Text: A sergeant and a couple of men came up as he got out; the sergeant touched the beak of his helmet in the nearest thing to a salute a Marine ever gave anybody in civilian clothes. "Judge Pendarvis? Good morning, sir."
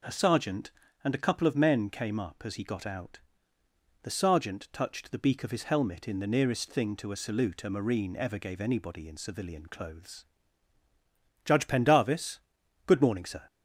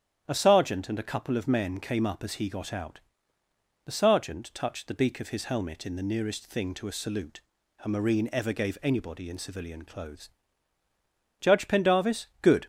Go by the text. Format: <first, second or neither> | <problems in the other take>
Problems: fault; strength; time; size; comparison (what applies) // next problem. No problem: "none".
first | starts louder than the rest; strong; until 1.2 s; 9.5 dB // pauses between "salute" and "a"; at 7.4 s; 0.42 s long // stops before "morning sir"; at 12.6 s